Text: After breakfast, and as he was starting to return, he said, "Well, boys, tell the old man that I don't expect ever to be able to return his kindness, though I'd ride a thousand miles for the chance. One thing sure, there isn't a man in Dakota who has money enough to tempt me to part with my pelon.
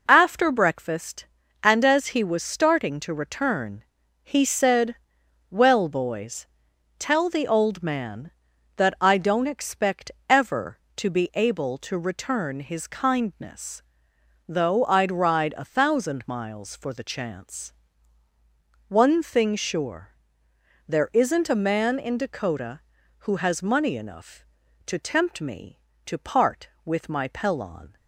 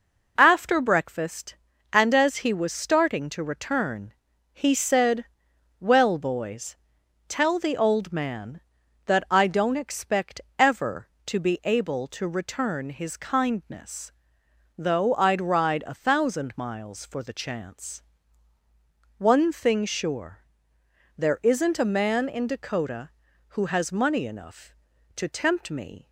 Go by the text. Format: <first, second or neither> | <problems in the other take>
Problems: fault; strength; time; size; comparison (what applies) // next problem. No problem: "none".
first | pauses between "expect" and "ever"; slight; at 10.4 s; 0.18 s long; slight in the first // stops before "to part with my pelon"; at 26.0 s